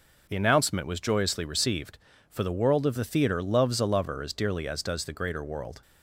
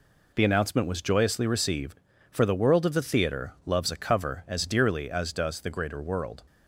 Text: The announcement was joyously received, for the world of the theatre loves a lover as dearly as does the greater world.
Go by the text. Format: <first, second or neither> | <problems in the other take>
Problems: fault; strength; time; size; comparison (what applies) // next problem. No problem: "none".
first | says "cover" for "lover"; at 3.9 s